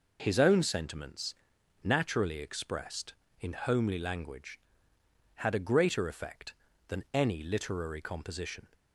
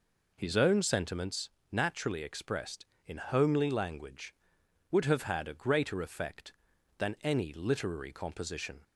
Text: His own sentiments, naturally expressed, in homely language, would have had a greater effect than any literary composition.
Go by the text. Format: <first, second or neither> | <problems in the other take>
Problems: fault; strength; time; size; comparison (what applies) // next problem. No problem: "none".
second | skips "would have"; at 4.9 s